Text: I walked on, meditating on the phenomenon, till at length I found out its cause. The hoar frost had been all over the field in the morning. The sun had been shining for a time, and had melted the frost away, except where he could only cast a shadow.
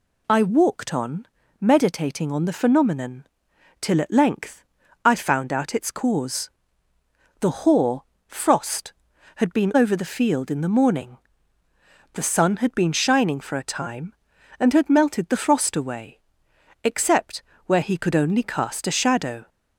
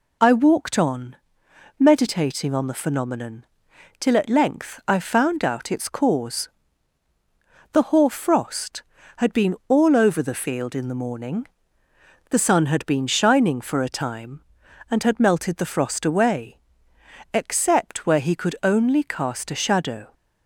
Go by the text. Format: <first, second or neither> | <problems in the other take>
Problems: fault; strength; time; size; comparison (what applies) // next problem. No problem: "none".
second | pauses between "length" and "I"; at 4.6 s; 0.40 s long // pauses between "hoar" and "frost"; slight; at 8.0 s; 0.22 s long // skips "all"; at 9.7 s // pauses between "except" and "where"; slight; at 17.4 s; 0.24 s long